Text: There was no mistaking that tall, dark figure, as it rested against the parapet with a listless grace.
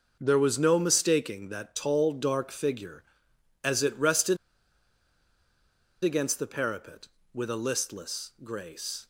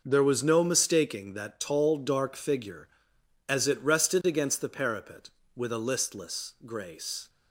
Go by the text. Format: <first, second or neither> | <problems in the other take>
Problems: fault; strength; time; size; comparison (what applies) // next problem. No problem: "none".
second | pauses between "rested" and "against"; strong; at 4.3 s; 1.6 s long